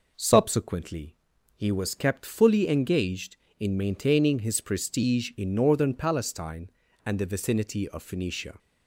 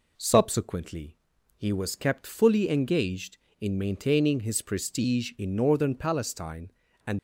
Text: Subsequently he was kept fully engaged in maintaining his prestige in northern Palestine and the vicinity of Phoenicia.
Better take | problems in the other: first | pauses between "Subsequently" and "he"; at 1.1 s; 0.40 s long; also in the first // stops before "the vicinity of Phoenicia"; at 7.1 s

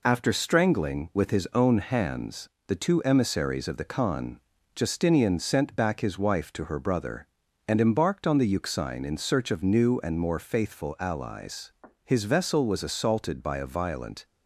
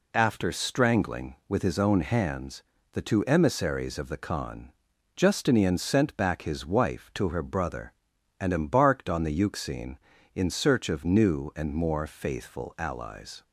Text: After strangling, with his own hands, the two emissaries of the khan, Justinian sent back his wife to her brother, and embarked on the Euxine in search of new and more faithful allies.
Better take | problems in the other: second | goes on to say "His vessel was assaulted by a violent"; strong; from 12.0 s on; 2.2 s long

